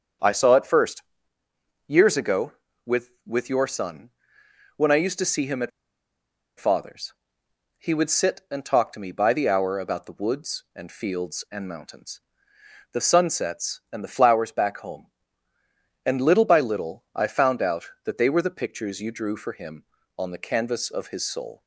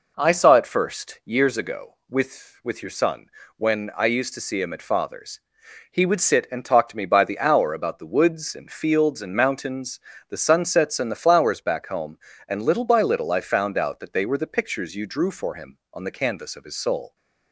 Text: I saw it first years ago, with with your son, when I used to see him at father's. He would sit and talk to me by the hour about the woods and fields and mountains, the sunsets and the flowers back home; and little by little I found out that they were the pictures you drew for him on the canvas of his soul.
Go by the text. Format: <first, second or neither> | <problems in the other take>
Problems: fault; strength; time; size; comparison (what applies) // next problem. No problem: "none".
second | starts louder than the rest; strong; until 2.0 s; 7.5 dB // pauses between "first" and "years"; noticeable; at 1.0 s; 0.86 s long // pauses between "at" and "father's"; noticeable; at 5.7 s; 0.87 s long